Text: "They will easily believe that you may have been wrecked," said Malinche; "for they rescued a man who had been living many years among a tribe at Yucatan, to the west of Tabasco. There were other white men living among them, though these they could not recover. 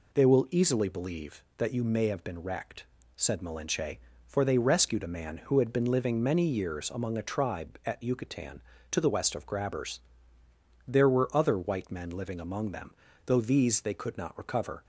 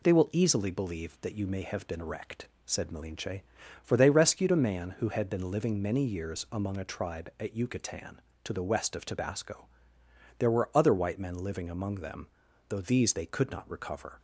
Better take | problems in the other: second | says "Grabbers" for "Tabasco"; at 9.4 s

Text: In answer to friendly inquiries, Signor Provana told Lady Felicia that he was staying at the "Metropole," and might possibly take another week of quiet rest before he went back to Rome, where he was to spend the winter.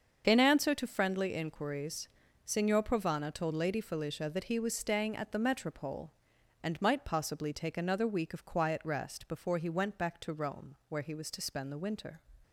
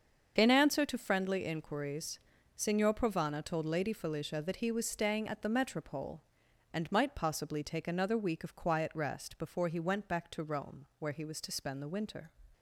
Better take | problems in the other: neither | starts louder than the rest; the same in both

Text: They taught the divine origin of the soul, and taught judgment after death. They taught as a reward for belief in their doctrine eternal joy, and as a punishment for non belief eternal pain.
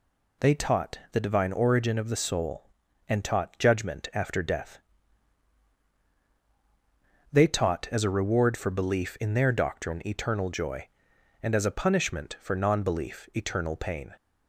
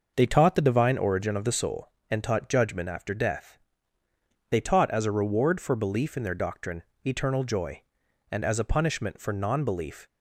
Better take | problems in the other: first | pauses between "doctrine" and "eternal"; slight; at 6.8 s; 0.24 s long // stops before "eternal pain"; at 10.0 s

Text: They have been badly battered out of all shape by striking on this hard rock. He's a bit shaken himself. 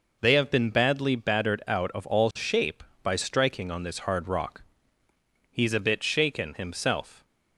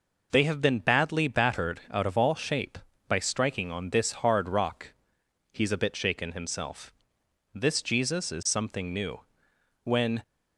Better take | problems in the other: first | goes on to say "This Jesus is something new When"; strong; from 7.5 s on; 2.6 s long

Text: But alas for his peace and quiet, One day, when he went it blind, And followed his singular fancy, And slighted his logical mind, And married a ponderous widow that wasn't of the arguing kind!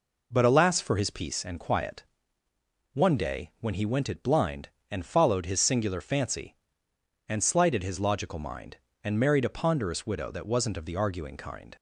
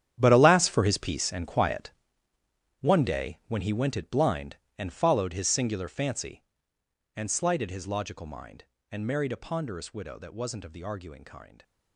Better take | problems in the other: first | gets quieter; strong; throughout; 14.5 dB

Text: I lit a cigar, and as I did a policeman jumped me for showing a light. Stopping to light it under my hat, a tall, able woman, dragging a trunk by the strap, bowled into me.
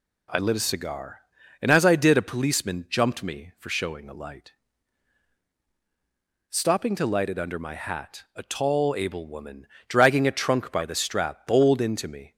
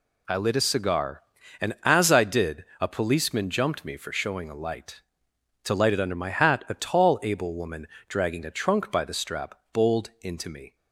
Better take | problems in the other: first | pauses between "did" and "a"; slight; at 2.6 s; 0.16 s long // skips "Stopping"; at 5.3 s

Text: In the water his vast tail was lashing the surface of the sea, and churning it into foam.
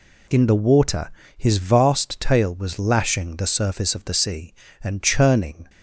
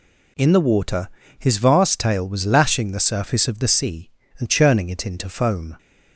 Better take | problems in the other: second | pauses between "water" and "his"; slight; at 1.0 s; 0.28 s long; slight in the second // stops before "it into foam"; at 5.6 s

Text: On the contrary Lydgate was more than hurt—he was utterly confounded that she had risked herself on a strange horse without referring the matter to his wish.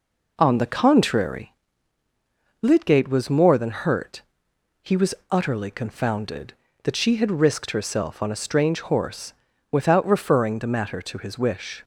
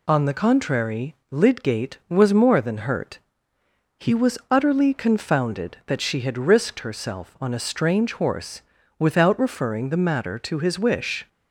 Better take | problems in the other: second | starts louder than the rest; noticeable; until 1.4 s; 4 dB // pauses between "contrary" and "Lydgate"; at 1.5 s; 1.0 s long; slight in the second // pauses between "was" and "utterly"; slight; at 5.1 s; 0.16 s long // pauses between "horse" and "without"; slight; at 9.3 s; 0.36 s long; slight in the second

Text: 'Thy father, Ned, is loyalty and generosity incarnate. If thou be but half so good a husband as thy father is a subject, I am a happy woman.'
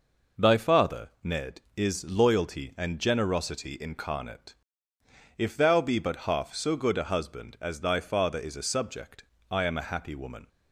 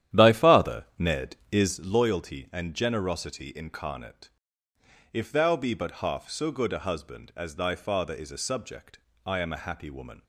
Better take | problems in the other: first | starts louder than the rest; strong; until 1.8 s; 11 dB

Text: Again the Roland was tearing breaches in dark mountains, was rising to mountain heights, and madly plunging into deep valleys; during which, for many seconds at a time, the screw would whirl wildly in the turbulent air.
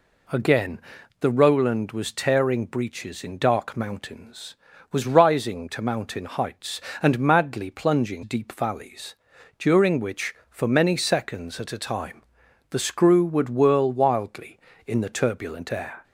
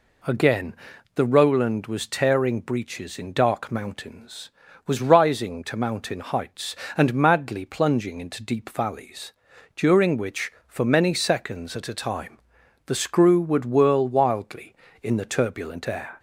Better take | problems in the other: second | pauses between "Again" and "the"; at 0.8 s; 0.40 s long; also in the second // skips "into"; at 8.2 s

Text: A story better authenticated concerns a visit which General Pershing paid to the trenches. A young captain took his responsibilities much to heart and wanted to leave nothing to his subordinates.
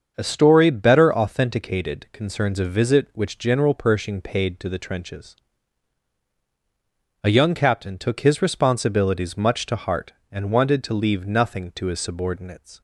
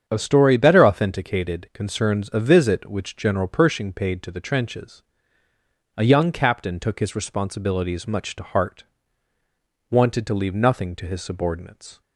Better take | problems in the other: first | starts louder than the rest; strong; until 1.0 s; 7.5 dB; also in the first // skips "and"; at 9.3 s

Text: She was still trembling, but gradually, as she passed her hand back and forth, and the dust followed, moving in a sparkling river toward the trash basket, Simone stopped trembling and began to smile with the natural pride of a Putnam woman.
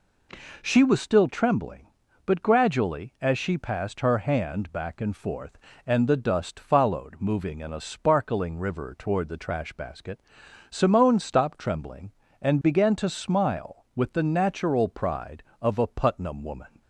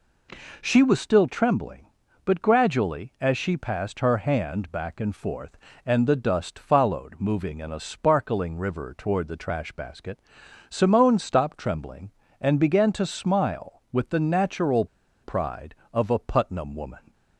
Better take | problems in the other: first | pauses between "natural" and "pride"; at 14.8 s; 0.37 s long

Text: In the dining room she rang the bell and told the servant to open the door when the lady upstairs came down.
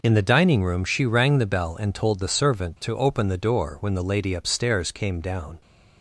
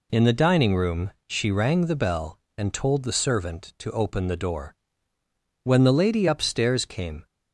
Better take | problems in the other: first | pauses between "room" and "she"; slight; at 1.1 s; 0.18 s long // pauses between "door" and "when"; noticeable; at 4.7 s; 0.88 s long // stops before "down"; at 7.2 s

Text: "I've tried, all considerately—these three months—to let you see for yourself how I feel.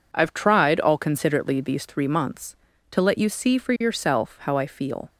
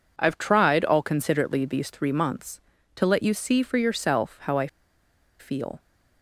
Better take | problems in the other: first | pauses between "I" and "feel"; noticeable; at 4.6 s; 0.71 s long

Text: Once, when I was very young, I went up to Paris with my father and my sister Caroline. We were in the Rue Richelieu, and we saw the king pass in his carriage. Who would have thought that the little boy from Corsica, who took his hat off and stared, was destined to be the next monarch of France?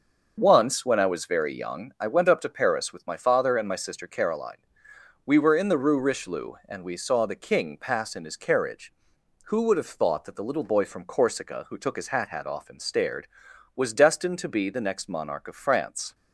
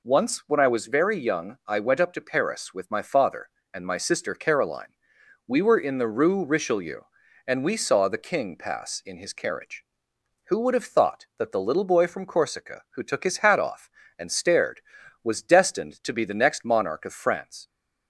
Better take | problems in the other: second | starts louder than the rest; until 1.3 s; 6 dB // says "hat" twice; at 12.2 s

